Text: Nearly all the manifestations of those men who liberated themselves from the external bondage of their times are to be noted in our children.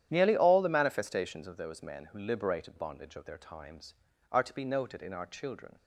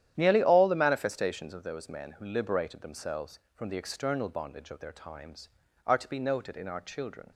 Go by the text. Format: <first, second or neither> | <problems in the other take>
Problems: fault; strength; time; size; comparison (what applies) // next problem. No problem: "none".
second | starts louder than the rest; strong; until 1.1 s; 10.5 dB; strong in the second // skips "themselves from the external"; at 2.7 s